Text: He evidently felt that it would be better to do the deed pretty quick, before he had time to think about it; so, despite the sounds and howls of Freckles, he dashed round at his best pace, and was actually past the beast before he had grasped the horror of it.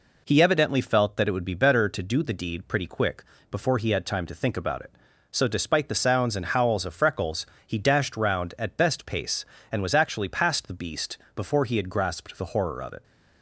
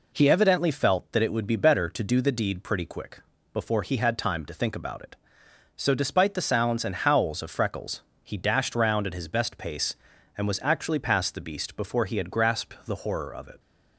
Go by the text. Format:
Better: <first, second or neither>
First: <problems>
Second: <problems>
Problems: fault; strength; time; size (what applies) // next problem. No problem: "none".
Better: second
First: skips "his"; at 8.7 s // pauses between "beast" and "before"; slight; at 11.1 s; 0.16 s long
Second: none